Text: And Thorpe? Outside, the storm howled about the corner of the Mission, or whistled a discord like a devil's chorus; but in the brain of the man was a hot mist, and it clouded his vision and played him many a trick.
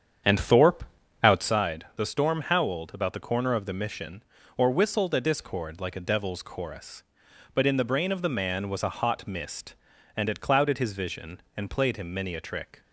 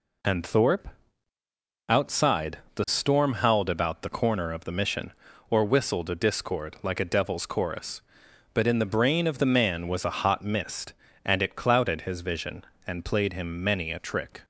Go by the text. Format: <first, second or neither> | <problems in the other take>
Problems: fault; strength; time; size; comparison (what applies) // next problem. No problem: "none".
second | starts louder than the rest; strong; until 1.6 s; 8 dB